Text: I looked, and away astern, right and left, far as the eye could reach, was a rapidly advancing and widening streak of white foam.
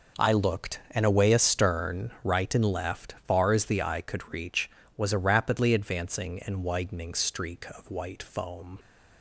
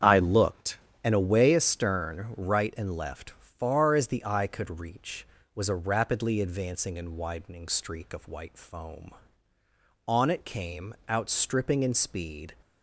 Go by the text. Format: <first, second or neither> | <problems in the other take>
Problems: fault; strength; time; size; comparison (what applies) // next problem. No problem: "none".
first | starts louder than the rest; strong; until 1.2 s; 8 dB // goes on to say "On it came outstripping in speed"; strong; from 10.0 s on; 2.4 s long